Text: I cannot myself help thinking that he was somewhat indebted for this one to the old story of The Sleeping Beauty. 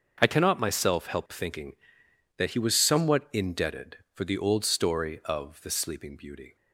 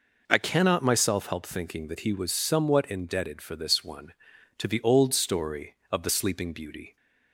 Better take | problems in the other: second | starts louder than the rest; until 1.2 s; 6.5 dB // skips "this one to"; at 4.2 s

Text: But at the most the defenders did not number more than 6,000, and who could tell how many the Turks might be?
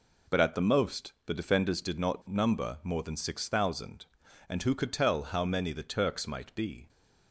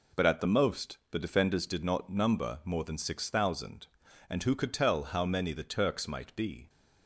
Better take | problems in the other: neither | none

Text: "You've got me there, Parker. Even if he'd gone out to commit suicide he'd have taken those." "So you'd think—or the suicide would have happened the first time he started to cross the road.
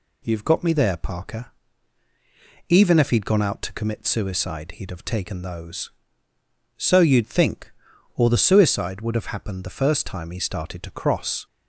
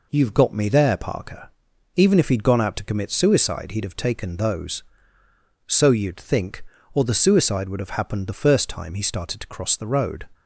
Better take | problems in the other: second | stops before "the road"; at 11.4 s

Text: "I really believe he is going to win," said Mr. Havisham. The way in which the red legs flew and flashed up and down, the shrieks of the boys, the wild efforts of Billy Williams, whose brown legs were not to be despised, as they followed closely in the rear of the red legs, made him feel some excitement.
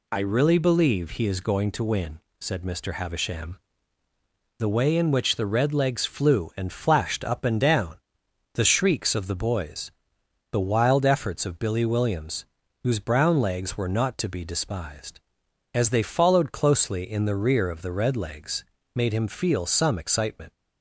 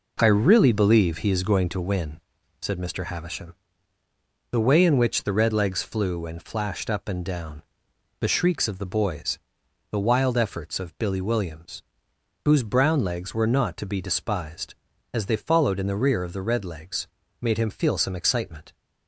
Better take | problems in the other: first | skips "closely"; at 15.7 s

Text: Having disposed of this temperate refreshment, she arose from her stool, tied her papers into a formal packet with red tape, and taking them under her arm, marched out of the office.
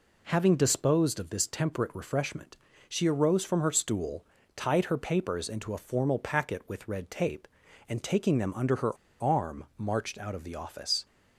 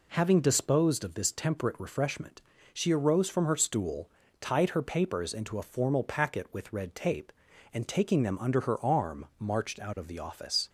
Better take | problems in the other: second | pauses between "her" and "arm"; slight; at 8.9 s; 0.26 s long

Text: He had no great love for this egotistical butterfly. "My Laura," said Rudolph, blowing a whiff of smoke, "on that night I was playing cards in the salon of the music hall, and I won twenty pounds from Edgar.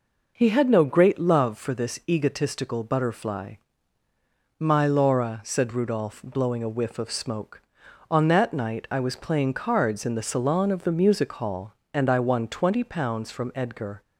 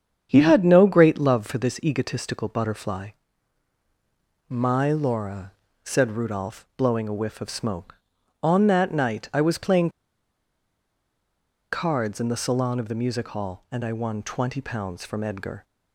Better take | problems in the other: first | starts louder than the rest; strong; until 1.3 s; 8 dB // pauses between "playing" and "cards"; strong; at 9.9 s; 1.8 s long

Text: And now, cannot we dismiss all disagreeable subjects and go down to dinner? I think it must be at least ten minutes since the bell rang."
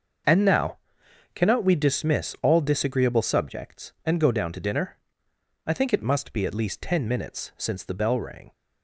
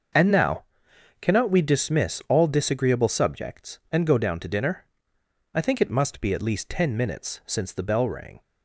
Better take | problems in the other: neither | starts louder than the rest; the same in both

